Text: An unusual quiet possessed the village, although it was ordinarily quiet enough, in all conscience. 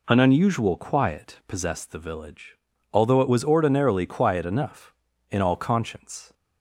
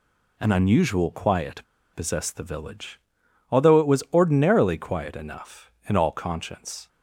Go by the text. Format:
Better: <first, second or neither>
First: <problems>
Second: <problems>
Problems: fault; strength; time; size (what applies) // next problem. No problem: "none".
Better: first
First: none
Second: pauses between "quiet" and "possessed"; slight; at 1.6 s; 0.32 s long